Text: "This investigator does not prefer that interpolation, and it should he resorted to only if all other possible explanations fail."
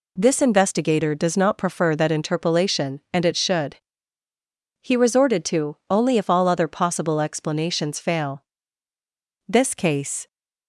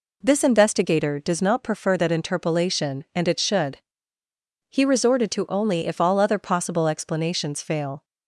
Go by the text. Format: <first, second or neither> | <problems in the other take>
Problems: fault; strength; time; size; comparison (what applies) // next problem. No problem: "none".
second | pauses between "should" and "he"; at 3.7 s; 1.0 s long; noticeable in the second // pauses between "to" and "only"; slight; at 5.7 s; 0.16 s long // goes on to say "This case"; noticeable; from 9.4 s on; 0.78 s long